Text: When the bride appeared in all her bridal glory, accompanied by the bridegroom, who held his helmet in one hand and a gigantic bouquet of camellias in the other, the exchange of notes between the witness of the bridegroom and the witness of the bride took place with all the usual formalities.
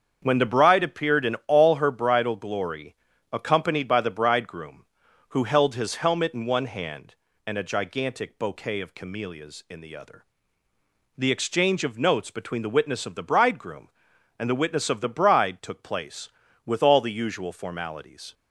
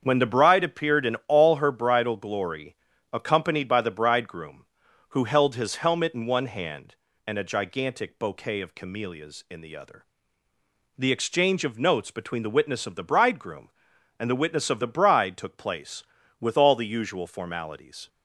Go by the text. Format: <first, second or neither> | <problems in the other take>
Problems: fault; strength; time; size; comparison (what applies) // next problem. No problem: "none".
neither | starts louder than the rest; the same in both